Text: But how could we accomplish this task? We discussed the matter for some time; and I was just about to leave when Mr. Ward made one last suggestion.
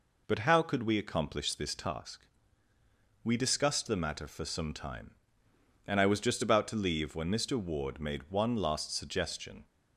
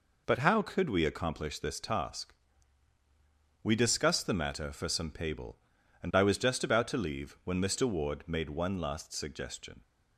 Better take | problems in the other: first | says "pable" for "time"; at 5.1 s

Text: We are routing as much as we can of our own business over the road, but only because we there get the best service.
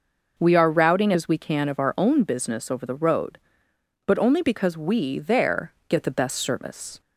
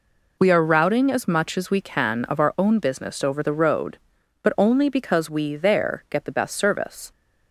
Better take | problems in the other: second | skips "as much"; at 1.1 s // pauses between "there" and "get"; slight; at 5.7 s; 0.16 s long

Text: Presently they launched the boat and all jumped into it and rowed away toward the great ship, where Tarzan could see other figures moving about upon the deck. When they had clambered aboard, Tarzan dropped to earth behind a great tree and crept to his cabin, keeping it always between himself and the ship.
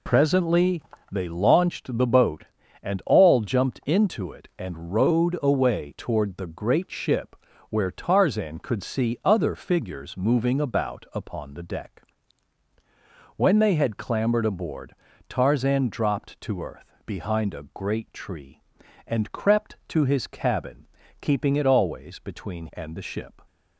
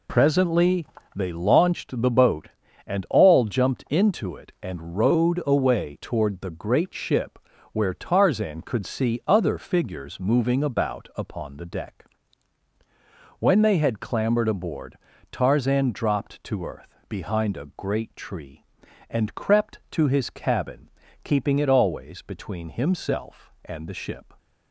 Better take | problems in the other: second | pauses between "Presently" and "they"; slight; at 0.8 s; 0.30 s long; slight in the second // skips "himself"; at 22.6 s

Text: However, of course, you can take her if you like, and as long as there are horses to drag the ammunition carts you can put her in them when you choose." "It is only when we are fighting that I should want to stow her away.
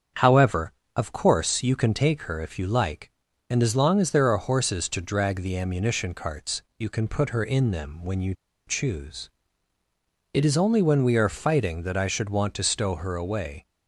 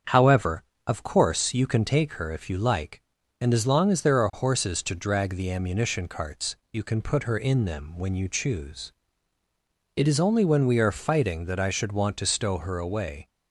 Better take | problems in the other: second | starts louder than the rest; strong; until 1.4 s; 7.5 dB; strong in the second // pauses between "carts" and "you"; slight; at 6.6 s; 0.16 s long; slight in the second // pauses between "you" and "choose"; slight; at 8.3 s; 0.34 s long

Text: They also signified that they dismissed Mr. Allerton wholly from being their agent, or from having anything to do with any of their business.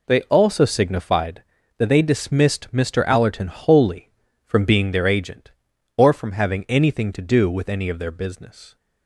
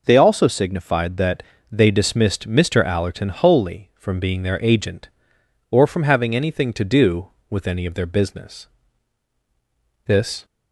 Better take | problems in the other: first | pauses between "that" and "they"; slight; at 1.4 s; 0.28 s long // goes on to say "This"; slight; from 10.0 s on; 0.40 s long

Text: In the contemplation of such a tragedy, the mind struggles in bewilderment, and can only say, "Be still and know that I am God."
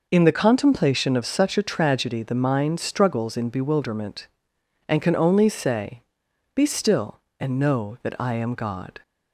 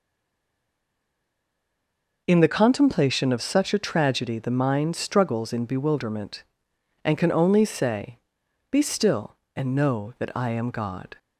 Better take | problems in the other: first | stays silent before the first word; until 2.2 s; 2.2 s long

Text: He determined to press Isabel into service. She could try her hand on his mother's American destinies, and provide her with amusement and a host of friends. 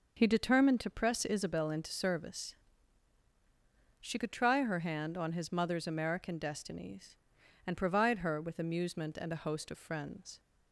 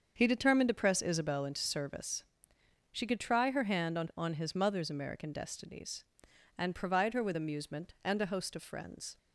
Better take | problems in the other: first | starts louder than the rest; until 1.1 s; 7 dB // says "on" twice; at 4.1 s

